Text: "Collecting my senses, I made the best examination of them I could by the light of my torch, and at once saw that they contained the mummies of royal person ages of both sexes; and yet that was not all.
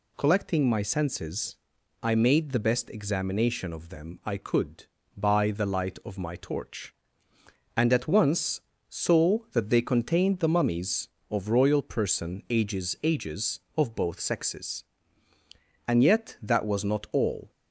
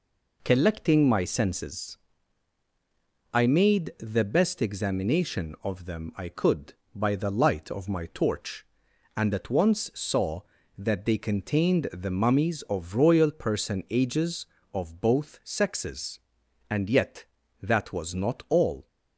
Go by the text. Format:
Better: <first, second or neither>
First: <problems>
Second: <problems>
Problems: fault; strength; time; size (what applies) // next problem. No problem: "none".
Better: second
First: pauses between "once" and "saw"; slight; at 8.5 s; 0.28 s long // says "ages" twice; at 13.0 s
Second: none